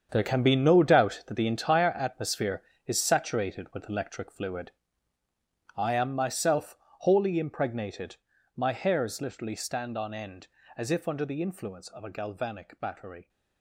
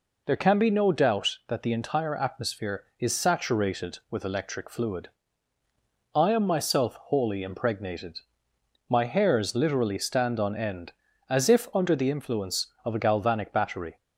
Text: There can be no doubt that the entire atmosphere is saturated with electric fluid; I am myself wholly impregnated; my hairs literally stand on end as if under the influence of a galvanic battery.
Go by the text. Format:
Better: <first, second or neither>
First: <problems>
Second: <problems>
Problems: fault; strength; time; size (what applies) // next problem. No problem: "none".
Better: second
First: gets quieter; strong; throughout; 12.5 dB // pauses between "myself" and "wholly"; slight; at 6.7 s; 0.26 s long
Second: none